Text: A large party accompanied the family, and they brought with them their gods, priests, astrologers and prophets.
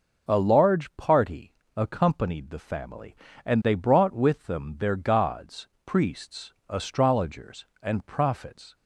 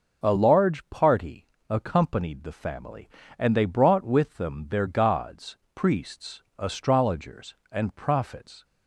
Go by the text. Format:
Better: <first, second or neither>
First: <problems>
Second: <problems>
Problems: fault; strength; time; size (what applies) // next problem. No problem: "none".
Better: neither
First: pauses between "party" and "accompanied"; slight; at 1.5 s; 0.24 s long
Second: pauses between "party" and "accompanied"; slight; at 1.4 s; 0.24 s long